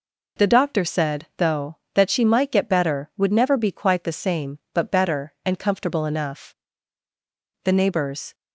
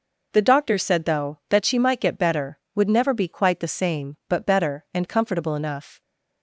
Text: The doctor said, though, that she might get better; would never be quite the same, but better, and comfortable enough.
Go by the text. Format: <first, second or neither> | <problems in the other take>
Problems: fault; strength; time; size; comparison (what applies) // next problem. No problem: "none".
second | goes on to say "The neighbors"; noticeable; from 7.6 s on; 0.70 s long